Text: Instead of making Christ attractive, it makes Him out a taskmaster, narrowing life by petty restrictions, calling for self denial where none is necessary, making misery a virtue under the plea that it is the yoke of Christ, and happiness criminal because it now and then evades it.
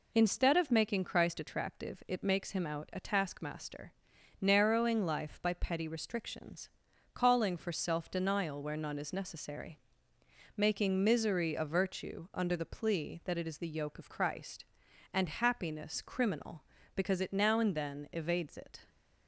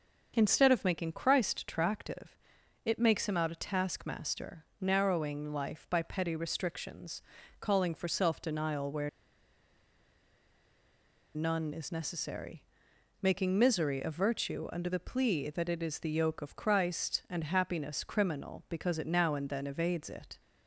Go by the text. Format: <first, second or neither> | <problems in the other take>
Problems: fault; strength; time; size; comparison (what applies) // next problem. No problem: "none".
first | starts louder than the rest; until 1.3 s; 6.5 dB // pauses between "where" and "none"; strong; at 9.0 s; 2.2 s long